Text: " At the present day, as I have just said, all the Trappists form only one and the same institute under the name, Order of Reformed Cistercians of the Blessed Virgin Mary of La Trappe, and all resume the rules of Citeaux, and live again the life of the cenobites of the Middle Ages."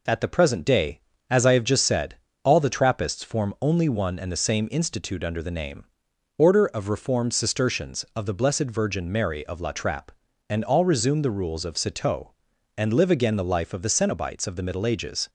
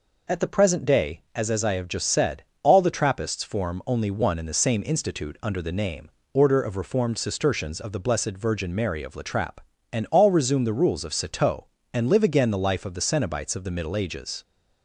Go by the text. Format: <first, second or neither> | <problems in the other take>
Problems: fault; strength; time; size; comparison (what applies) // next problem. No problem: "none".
first | says "as" twice; at 1.4 s